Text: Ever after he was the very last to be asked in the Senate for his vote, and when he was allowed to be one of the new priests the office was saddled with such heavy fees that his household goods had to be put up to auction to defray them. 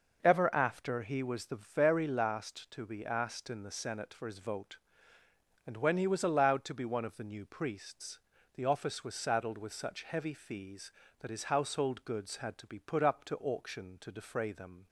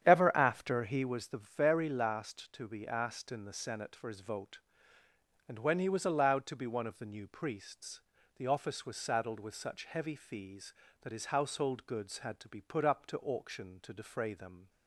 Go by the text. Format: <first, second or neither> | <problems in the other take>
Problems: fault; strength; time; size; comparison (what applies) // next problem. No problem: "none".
first | starts louder than the rest; strong; until 1.2 s; 9 dB // pauses between "priests" and "the"; slight; at 7.9 s; 0.36 s long; slight in the first